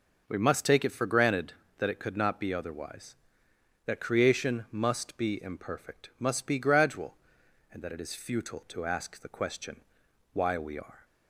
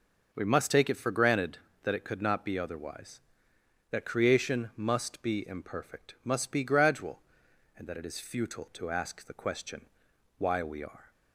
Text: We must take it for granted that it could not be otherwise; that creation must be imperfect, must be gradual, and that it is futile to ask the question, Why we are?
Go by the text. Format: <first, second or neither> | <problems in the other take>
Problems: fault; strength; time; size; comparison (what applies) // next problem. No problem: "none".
neither | none